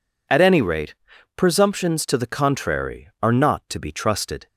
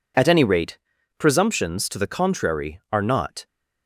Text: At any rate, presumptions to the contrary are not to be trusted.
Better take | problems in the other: first | stops before "to be trusted"; at 3.4 s

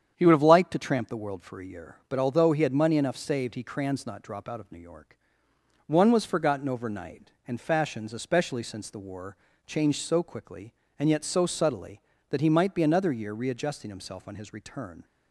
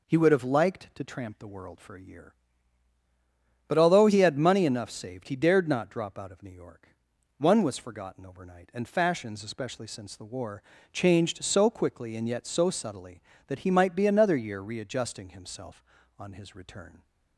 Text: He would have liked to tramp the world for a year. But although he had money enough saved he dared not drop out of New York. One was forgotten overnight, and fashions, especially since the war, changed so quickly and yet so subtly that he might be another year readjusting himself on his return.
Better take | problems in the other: second | starts louder than the rest; strong; until 1.1 s; 8.5 dB // says "crans" for "dared"; at 3.6 s

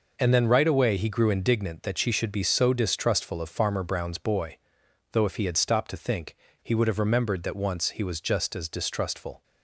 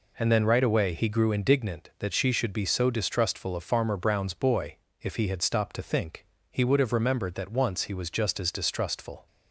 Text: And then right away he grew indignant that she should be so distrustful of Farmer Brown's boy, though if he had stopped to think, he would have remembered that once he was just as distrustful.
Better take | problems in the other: first | skips "though"; at 4.8 s

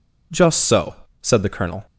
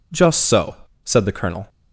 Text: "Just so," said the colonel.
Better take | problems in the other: neither | none

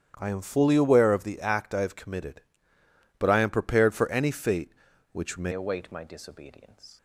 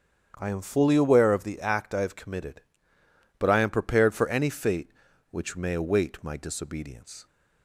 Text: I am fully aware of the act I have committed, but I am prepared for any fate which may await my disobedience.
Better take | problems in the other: second | starts louder than the rest; strong; until 1.1 s; 9 dB; strong in the second // changes voice at "await"; from 5.5 s on; 1.4 s long

